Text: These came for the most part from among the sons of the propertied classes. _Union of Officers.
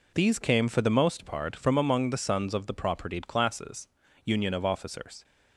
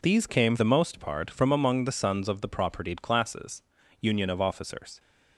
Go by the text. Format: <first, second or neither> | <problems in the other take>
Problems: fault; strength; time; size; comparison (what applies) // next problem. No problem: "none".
first | skips "for"; at 0.5 s